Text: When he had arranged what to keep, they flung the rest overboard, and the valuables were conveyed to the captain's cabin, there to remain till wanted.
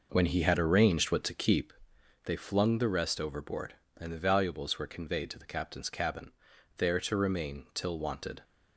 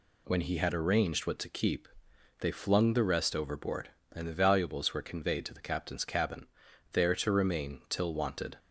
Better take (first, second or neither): second